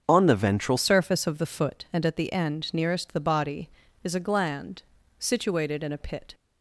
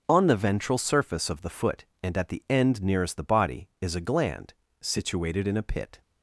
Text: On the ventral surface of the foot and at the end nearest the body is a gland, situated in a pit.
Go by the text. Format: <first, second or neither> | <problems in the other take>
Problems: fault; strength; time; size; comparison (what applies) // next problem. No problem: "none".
second | starts louder than the rest; until 1.0 s; 7 dB // changes voice at "surface"; from 0.7 s on; 5.6 s long